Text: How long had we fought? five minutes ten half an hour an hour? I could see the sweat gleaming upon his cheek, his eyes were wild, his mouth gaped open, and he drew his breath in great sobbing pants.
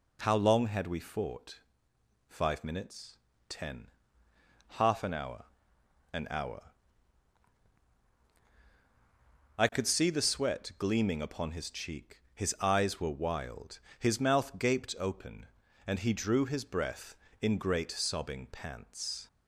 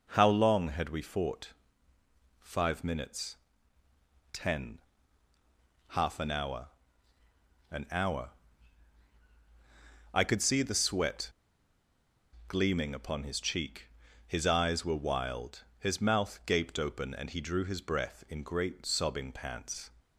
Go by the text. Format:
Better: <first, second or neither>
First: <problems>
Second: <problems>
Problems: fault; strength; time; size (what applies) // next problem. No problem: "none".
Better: first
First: pauses between "minutes" and "ten"; slight; at 3.1 s; 0.32 s long // pauses between "ten" and "half"; noticeable; at 3.8 s; 0.84 s long // pauses between "hour" and "an"; noticeable; at 5.4 s; 0.68 s long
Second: pauses between "minutes" and "ten"; noticeable; at 3.3 s; 0.96 s long // pauses between "ten" and "half"; at 4.7 s; 1.1 s long // pauses between "hour" and "an"; at 6.6 s; 1.0 s long // pauses between "sweat" and "gleaming"; at 11.3 s; 1.1 s long